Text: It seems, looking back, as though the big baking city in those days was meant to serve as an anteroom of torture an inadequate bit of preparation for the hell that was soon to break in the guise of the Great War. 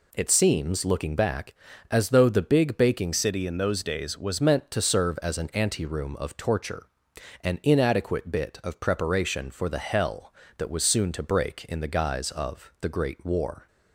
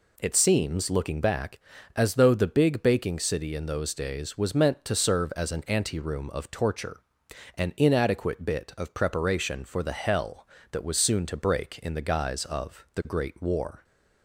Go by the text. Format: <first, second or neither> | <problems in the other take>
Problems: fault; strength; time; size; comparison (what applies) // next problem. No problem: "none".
second | changes voice from "city" to "was"; from 3.1 to 4.3 s; 1.2 s long // pauses between "torture" and "an"; noticeable; at 6.8 s; 0.54 s long; noticeable in the second